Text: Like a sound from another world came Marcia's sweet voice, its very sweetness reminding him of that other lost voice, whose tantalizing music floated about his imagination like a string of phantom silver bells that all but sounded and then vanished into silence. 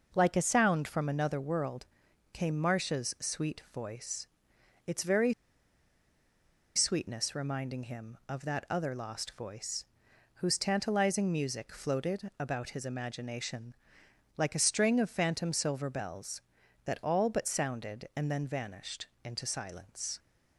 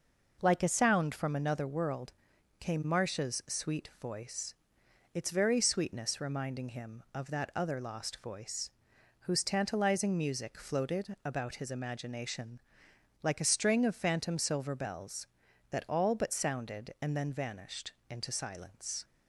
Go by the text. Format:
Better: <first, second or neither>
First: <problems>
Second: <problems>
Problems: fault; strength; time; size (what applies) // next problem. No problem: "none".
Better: second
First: pauses between "world" and "came"; noticeable; at 1.8 s; 0.48 s long // pauses between "very" and "sweetness"; strong; at 5.3 s; 1.4 s long // pauses between "imagination" and "like"; noticeable; at 13.7 s; 0.60 s long // pauses between "vanished" and "into"; slight; at 19.0 s; 0.18 s long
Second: pauses between "world" and "came"; noticeable; at 2.1 s; 0.48 s long // pauses between "imagination" and "like"; noticeable; at 12.6 s; 0.60 s long // pauses between "vanished" and "into"; slight; at 17.9 s; 0.18 s long